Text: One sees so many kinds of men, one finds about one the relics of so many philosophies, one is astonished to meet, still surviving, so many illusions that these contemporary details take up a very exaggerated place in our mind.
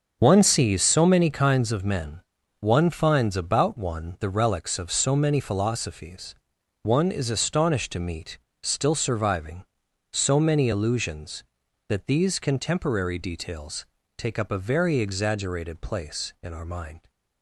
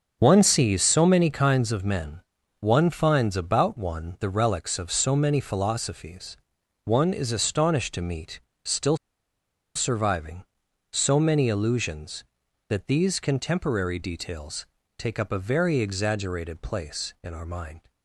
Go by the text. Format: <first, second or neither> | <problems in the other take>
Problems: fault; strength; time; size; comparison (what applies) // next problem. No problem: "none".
first | starts louder than the rest; until 1.2 s; 6.5 dB; also in the first // pauses between "still" and "surviving"; noticeable; at 8.9 s; 0.79 s long // pauses between "details" and "take"; slight; at 14.6 s; 0.32 s long; slight in the first